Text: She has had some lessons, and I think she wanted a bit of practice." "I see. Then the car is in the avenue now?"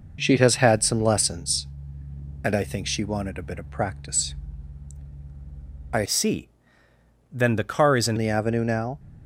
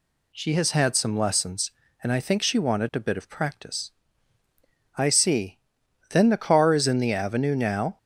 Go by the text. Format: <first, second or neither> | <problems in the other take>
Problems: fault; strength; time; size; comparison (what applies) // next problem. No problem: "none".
second | changes voice from "see" to "in"; from 6.0 to 8.1 s; 2.1 s long